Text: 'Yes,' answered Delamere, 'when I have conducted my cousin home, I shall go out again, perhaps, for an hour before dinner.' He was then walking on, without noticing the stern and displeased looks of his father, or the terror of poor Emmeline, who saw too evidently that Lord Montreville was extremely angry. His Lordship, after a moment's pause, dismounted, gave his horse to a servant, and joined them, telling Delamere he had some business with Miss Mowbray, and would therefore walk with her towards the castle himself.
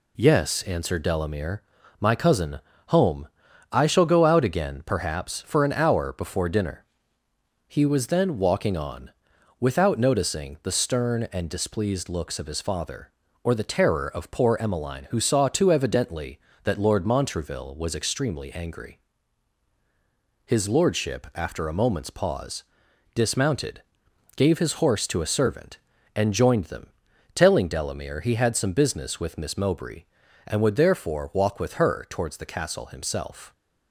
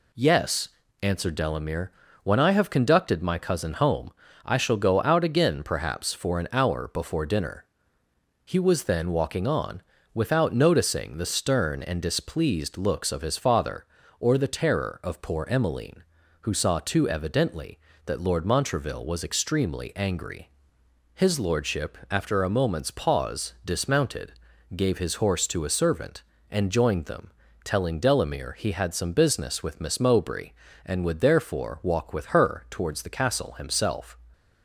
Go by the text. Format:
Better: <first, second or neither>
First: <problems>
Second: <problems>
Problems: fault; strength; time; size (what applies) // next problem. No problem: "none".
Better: second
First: skips "when I have conducted"; at 1.8 s // pauses between "cousin" and "home"; slight; at 2.6 s; 0.28 s long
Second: none